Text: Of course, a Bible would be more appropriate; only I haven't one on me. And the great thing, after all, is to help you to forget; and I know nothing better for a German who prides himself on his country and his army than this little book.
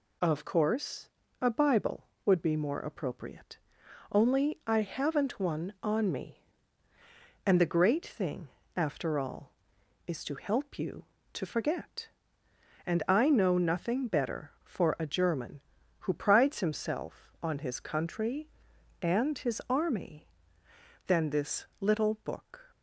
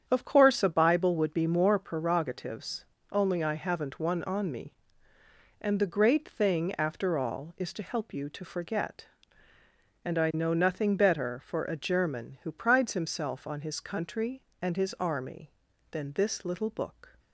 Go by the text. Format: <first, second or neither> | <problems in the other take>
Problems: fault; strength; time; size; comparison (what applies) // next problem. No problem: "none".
first | starts louder than the rest; strong; until 1.0 s; 8.5 dB // says "prerogatives" for "appropriate"; at 1.8 s